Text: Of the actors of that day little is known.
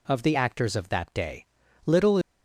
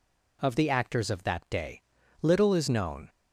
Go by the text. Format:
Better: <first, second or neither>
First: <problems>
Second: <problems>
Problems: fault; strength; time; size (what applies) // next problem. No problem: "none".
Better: second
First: pauses between "day" and "little"; at 1.4 s; 0.40 s long // stops before "is known"; at 2.2 s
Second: pauses between "day" and "little"; at 1.8 s; 0.40 s long